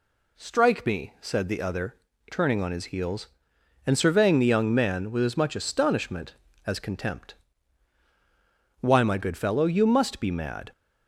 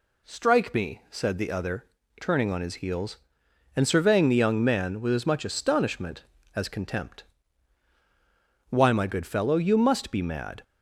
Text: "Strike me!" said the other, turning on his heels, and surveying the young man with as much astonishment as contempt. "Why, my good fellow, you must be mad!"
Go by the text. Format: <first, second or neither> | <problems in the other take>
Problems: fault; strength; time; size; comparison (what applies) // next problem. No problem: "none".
neither | none